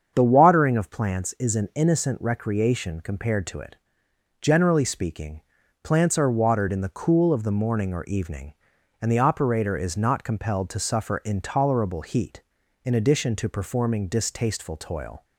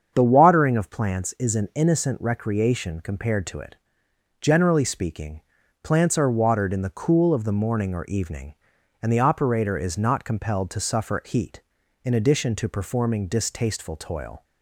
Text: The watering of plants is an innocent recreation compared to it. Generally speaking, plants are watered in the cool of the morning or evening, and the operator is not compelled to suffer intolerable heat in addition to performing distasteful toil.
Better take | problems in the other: first | starts louder than the rest; strong; until 1.1 s; 7.5 dB; strong in the first // skips "intolerable"; at 11.2 s

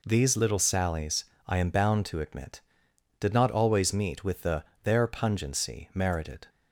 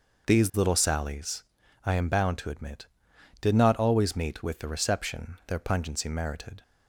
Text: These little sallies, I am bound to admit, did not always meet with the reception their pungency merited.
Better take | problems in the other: second | skips "reception"; at 4.7 s

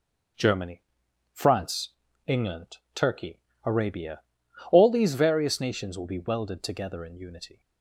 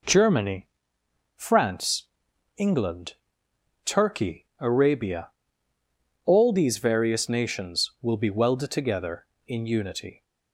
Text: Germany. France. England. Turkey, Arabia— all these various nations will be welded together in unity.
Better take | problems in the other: neither | none

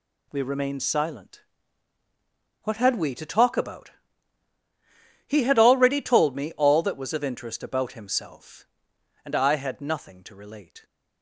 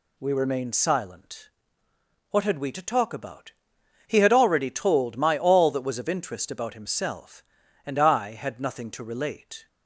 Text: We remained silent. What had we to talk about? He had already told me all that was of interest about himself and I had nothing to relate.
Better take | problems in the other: first | says "my" for "me"; at 5.1 s

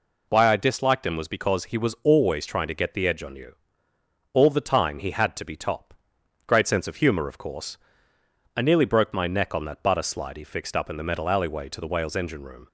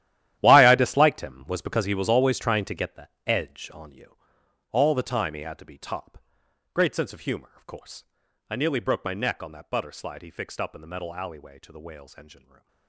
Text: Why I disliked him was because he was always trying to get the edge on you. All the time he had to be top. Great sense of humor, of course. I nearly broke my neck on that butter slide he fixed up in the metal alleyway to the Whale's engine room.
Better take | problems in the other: first | gets quieter; strong; throughout; 15.5 dB // pauses between "the" and "edge"; slight; at 3.0 s; 0.18 s long // stays silent after the last word; slight; from 12.3 s on; 0.5 s long

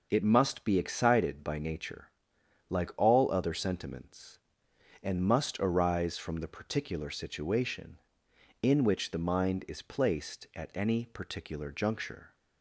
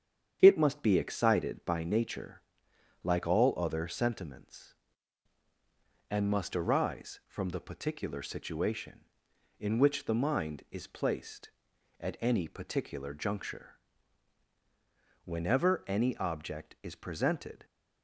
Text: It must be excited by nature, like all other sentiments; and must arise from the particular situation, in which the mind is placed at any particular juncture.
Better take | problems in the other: first | starts louder than the rest; strong; until 1.4 s; 8.5 dB // goes on to say "Whenever any object is presented"; strong; from 15.2 s on; 2.4 s long

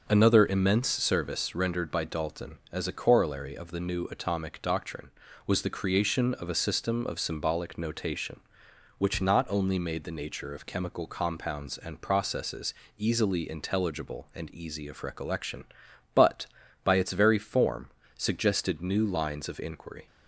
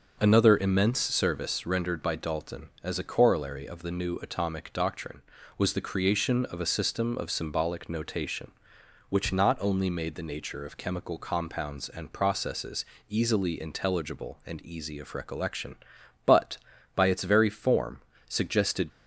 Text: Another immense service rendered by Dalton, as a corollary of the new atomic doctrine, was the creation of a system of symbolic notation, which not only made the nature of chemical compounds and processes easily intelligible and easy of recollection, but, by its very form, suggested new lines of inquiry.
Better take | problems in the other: first | starts louder than the rest; noticeable; until 1.2 s; 6 dB; noticeable in the first // pauses between "processes" and "easily"; slight; at 12.8 s; 0.24 s long; slight in the first // stops before "new lines of inquiry"; at 18.9 s

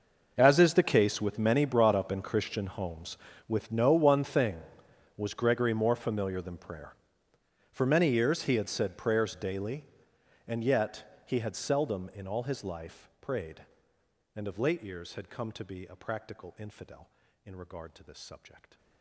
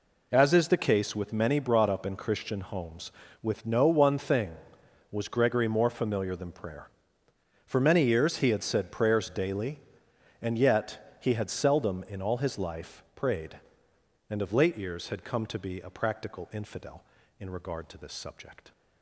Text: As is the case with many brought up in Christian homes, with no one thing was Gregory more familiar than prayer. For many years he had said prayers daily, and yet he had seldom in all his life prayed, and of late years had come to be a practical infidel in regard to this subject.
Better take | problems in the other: second | gets quieter; strong; throughout; 20 dB

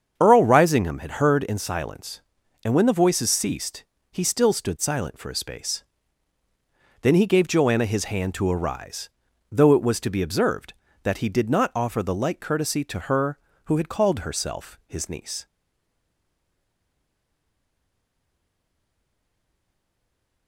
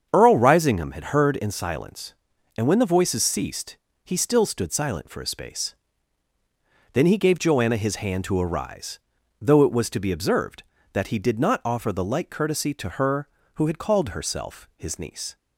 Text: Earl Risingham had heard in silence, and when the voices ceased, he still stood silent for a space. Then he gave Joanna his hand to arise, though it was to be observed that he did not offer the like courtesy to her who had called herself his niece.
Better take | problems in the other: second | starts louder than the rest; strong; until 1.1 s; 7 dB; strong in the second // stays silent after the last word; strong; from 15.4 s on; 5.0 s long

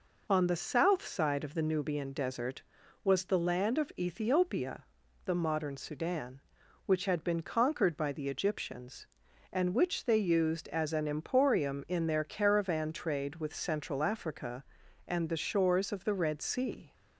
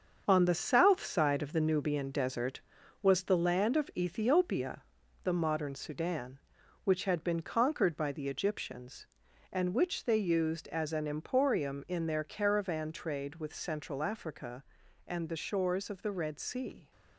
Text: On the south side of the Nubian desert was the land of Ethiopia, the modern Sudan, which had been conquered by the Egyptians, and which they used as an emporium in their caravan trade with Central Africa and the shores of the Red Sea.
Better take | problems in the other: first | gets quieter; throughout; 7 dB

